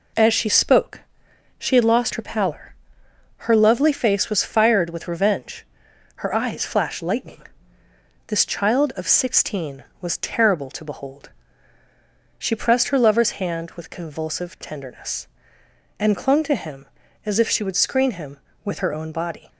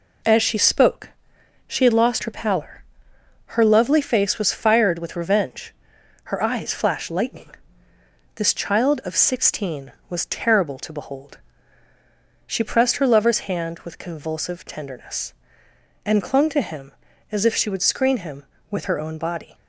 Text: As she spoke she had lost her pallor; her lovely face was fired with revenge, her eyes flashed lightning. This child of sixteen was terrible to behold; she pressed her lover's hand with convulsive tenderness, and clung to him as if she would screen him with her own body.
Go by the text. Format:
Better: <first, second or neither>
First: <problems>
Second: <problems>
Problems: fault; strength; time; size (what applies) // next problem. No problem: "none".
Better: neither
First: pauses between "spoke" and "she"; noticeable; at 0.9 s; 0.58 s long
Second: pauses between "spoke" and "she"; noticeable; at 1.0 s; 0.58 s long